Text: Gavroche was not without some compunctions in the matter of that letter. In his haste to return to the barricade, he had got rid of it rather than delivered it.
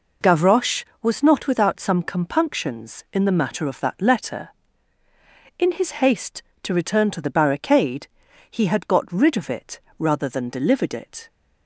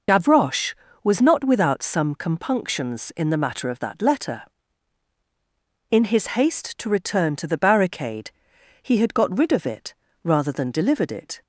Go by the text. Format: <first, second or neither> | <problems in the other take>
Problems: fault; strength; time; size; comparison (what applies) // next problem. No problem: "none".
first | loses the start of "Gavroche"; at 0.0 s; 25 ms // pauses between "it" and "rather"; slight; at 9.9 s; 0.30 s long; slight in the first